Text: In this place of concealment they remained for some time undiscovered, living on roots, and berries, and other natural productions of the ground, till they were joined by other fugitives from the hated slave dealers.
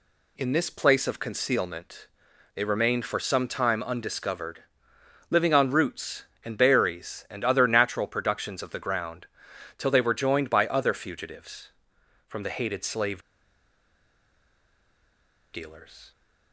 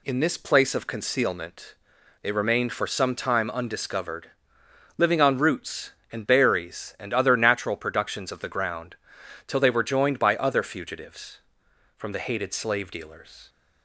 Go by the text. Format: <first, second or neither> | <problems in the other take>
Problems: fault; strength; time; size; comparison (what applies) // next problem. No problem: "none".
second | pauses between "concealment" and "they"; noticeable; at 2.0 s; 0.48 s long; noticeable in the second // pauses between "slave" and "dealers"; strong; at 13.2 s; 2.3 s long